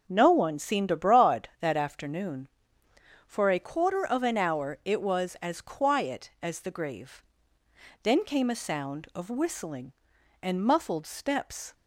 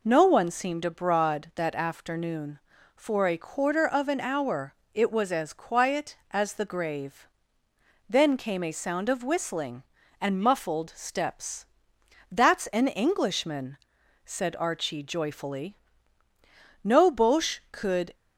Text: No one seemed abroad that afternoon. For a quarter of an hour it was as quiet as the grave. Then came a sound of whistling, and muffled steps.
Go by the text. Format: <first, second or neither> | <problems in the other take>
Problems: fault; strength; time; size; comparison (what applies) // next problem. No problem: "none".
first | pauses between "hour" and "it"; slight; at 4.7 s; 0.20 s long // goes on to say "That's an Englishman said Archie joyfully No Boche could"; strong; from 12.3 s on; 5.8 s long